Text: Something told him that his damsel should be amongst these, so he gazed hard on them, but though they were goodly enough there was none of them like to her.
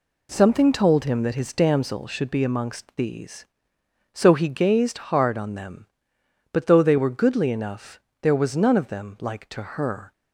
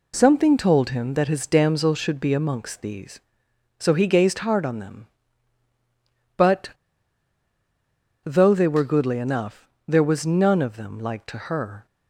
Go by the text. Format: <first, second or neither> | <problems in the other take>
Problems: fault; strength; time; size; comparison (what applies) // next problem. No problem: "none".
first | pauses between "but" and "though"; strong; at 6.6 s; 1.5 s long // pauses between "enough" and "there"; slight; at 9.6 s; 0.20 s long; slight in the first